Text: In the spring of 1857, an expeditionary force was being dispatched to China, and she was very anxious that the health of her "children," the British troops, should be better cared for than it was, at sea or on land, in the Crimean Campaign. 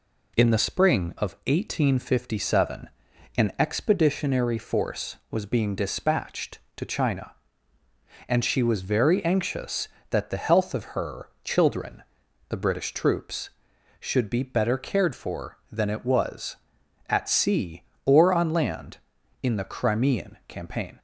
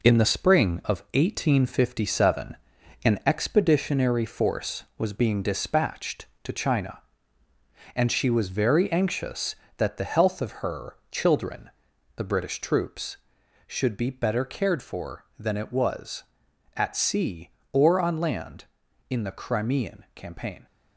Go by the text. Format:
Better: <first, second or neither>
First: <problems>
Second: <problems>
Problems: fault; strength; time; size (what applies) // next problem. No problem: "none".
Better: first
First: pauses between "her" and "children"; slight; at 11.2 s; 0.16 s long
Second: gets quieter; throughout; 6 dB // pauses between "her" and "children"; slight; at 10.9 s; 0.16 s long